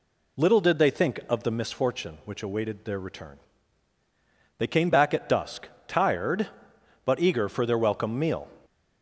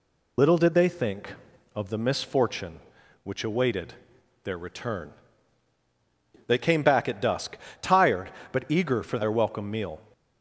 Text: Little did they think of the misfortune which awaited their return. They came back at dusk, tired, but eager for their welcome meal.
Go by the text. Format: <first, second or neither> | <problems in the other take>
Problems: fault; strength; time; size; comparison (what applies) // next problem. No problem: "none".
first | loses the start of "Little"; at 0.3 s; 40 ms // pauses between "awaited" and "their"; noticeable; at 3.9 s; 0.50 s long